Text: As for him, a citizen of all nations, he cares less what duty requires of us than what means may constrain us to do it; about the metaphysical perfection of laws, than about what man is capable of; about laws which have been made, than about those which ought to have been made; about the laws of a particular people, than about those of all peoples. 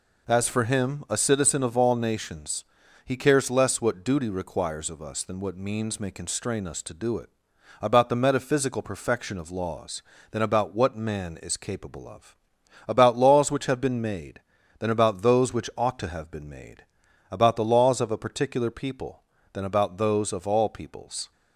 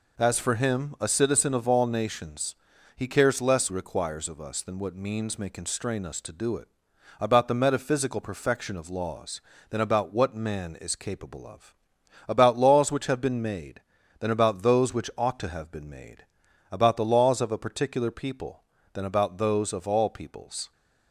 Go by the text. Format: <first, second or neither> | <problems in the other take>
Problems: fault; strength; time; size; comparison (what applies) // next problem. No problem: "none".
first | skips "what duty"; at 3.7 s